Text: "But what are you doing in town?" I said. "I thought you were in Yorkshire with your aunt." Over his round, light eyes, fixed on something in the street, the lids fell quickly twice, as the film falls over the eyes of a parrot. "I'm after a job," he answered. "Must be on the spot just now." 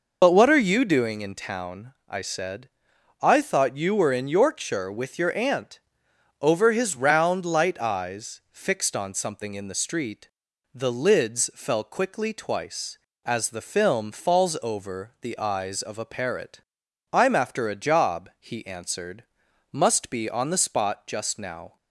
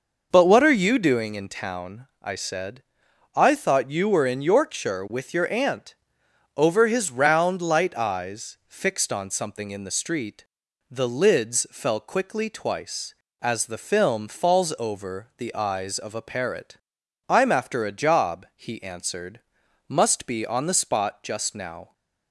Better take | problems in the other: second | loses the start of "But"; at 0.2 s; 40 ms

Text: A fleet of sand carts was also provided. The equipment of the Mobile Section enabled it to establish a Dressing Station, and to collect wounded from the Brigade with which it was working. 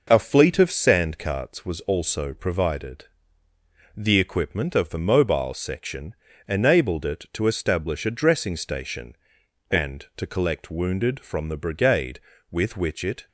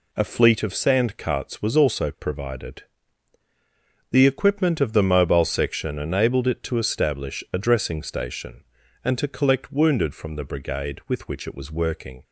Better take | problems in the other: second | pauses between "Section" and "enabled"; slight; at 6.1 s; 0.34 s long // stops before "was working"; at 13.2 s

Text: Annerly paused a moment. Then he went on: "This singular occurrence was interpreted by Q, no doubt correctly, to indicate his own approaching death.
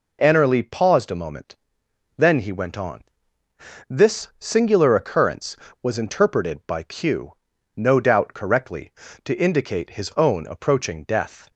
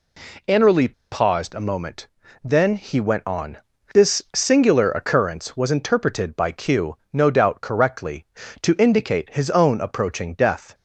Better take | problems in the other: first | pauses between "Annerly" and "paused"; slight; at 0.9 s; 0.19 s long

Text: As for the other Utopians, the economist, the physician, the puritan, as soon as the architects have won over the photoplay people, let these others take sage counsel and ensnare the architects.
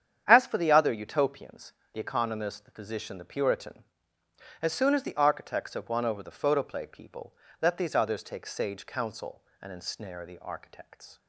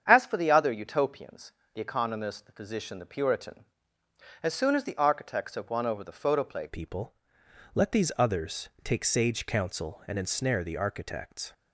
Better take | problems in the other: first | starts louder than the rest; strong; until 1.0 s; 8 dB; strong in the first // changes voice at "people"; from 6.6 s on; 4.9 s long // pauses between "others" and "take"; slight; at 8.6 s; 0.16 s long

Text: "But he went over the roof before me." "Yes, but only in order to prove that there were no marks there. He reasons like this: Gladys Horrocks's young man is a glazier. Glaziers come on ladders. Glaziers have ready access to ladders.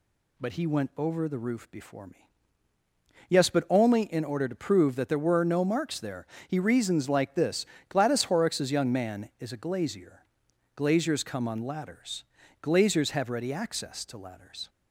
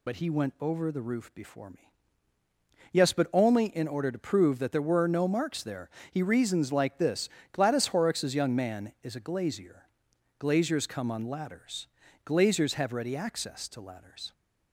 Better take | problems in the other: first | loses the start of "But"; at 0.0 s; 45 ms

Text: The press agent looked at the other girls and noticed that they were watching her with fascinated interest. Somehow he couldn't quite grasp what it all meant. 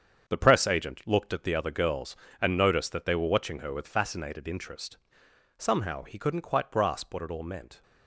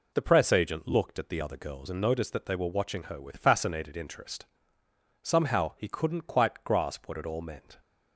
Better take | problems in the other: second | gets quieter; strong; throughout; 9 dB

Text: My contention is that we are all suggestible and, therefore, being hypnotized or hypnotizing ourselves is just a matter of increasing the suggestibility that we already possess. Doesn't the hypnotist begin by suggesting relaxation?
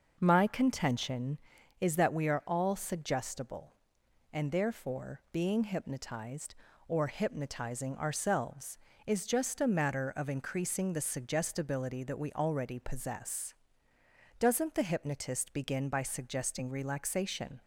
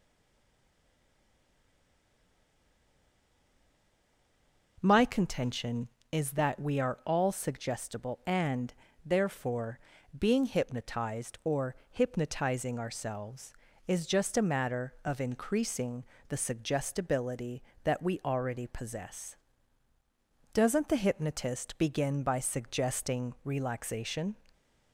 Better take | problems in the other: first | stays silent before the first word; strong; until 4.7 s; 4.7 s long // pauses between "or" and "hypnotizing"; slight; at 11.7 s; 0.16 s long // pauses between "increasing" and "the"; slight; at 16.0 s; 0.24 s long

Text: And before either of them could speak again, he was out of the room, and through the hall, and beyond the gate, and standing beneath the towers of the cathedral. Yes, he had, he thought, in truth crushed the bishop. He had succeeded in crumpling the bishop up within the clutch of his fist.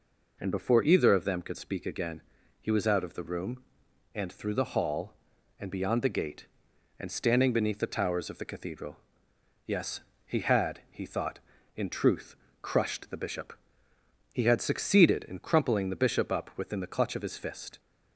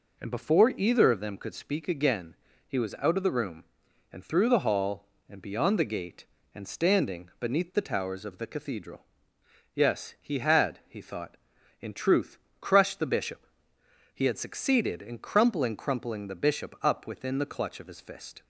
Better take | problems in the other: first | pauses between "truth" and "crushed"; slight; at 12.3 s; 0.22 s long; slight in the first // says "crumpling" twice; at 15.7 s

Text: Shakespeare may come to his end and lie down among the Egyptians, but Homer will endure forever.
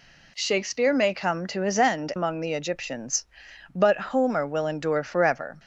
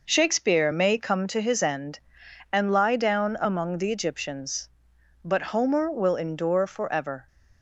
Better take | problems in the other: second | skips "and lie down"; at 2.1 s

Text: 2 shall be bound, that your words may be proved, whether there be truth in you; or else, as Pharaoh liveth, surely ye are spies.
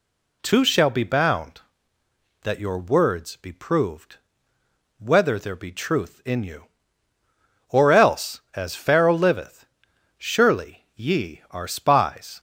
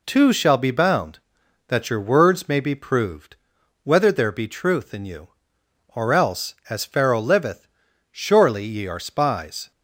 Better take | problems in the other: second | skips "may"; at 3.3 s

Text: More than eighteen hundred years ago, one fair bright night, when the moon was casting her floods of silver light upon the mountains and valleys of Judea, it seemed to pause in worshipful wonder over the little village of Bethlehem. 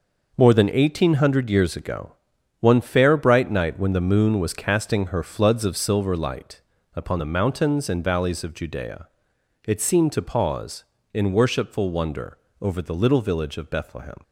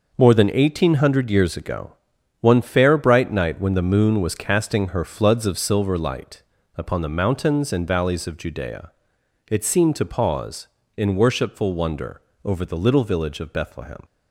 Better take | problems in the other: neither | pauses between "light" and "upon"; slight; the same in both // pauses between "wonder" and "over"; slight; the same in both

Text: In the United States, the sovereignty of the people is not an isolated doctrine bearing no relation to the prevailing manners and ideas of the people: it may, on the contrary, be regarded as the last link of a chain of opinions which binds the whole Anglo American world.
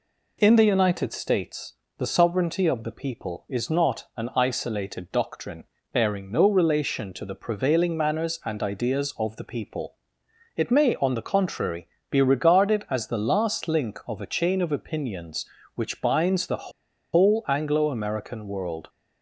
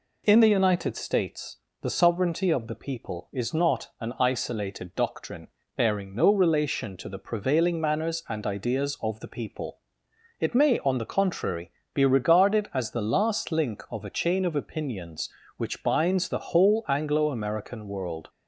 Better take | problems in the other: second | pauses between "doctrine" and "bearing"; slight; at 5.6 s; 0.26 s long; slight in the second // pauses between "the" and "whole"; at 16.7 s; 0.42 s long

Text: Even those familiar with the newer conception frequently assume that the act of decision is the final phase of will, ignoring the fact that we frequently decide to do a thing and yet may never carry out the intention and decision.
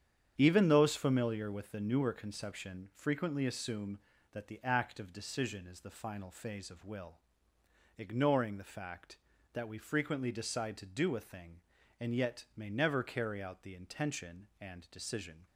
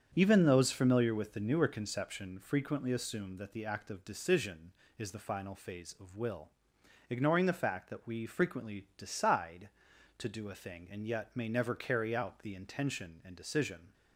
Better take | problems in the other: neither | starts louder than the rest; strong; the same in both

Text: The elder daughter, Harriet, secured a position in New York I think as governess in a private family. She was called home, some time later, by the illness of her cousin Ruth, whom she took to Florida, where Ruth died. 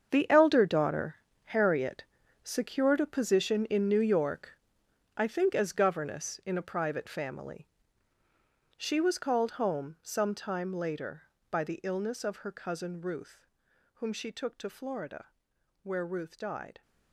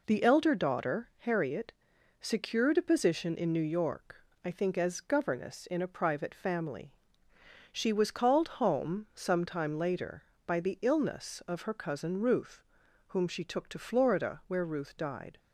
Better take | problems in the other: second | gets quieter; strong; throughout; 13 dB // pauses between "York" and "I"; noticeable; at 4.5 s; 0.66 s long; slight in the second

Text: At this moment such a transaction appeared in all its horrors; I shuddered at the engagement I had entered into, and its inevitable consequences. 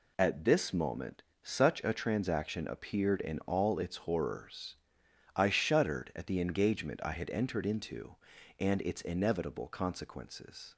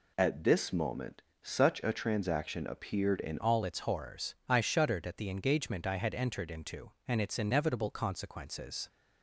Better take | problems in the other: first | pauses between "moment" and "such"; slight; at 1.2 s; 0.20 s long; slight in the first // changes voice at "all"; from 3.4 s on; 5.4 s long

